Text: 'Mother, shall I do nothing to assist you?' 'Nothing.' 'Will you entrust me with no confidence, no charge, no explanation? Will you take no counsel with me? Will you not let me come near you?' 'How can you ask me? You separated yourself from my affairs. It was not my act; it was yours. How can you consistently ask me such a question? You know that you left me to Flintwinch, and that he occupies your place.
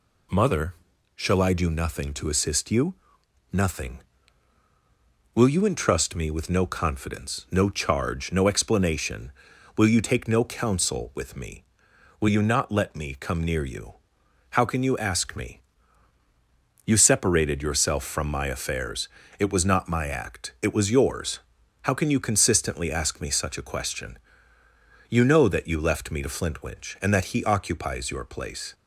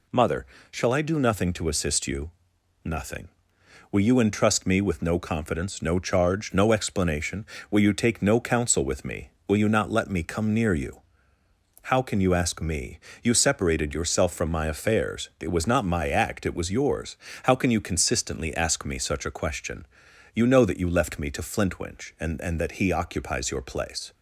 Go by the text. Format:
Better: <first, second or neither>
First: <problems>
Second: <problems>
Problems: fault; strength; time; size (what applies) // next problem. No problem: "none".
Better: first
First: none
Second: says "and" twice; at 22.4 s